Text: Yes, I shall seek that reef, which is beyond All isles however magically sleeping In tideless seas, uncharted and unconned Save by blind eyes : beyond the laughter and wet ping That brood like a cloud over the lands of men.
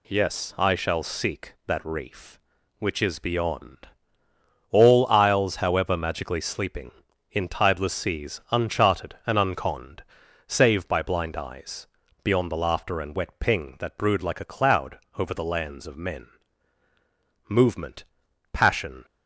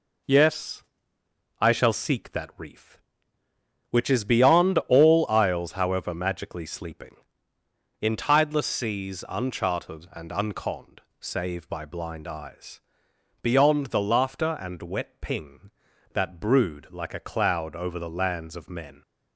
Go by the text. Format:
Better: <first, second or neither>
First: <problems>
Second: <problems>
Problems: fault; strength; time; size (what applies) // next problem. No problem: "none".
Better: second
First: pauses between "beyond" and "All"; noticeable; at 3.8 s; 0.84 s long // pauses between "unconned" and "Save"; at 10.0 s; 0.44 s long // pauses between "cloud" and "over"; slight; at 14.9 s; 0.18 s long // goes on to say "Movement passion"; from 17.4 s on; 1.5 s long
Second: pauses between "unconned" and "Save"; slight; at 11.0 s; 0.18 s long